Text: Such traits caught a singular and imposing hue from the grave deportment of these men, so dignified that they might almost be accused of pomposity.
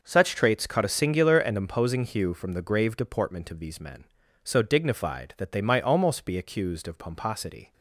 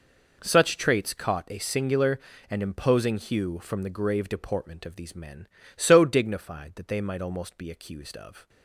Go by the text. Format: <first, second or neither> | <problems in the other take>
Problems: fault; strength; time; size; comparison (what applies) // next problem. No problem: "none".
first | stops before "pomposity"; at 8.4 s